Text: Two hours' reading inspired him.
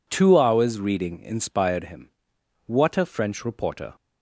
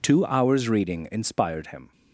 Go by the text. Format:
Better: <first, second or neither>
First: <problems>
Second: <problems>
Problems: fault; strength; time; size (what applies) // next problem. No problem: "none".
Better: second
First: goes on to say "What a French reporter"; noticeable; from 2.6 s on; 1.2 s long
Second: none